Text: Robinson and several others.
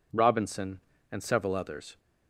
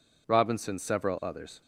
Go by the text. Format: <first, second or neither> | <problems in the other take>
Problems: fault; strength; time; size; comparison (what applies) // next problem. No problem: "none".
first | skips "and"; at 0.7 s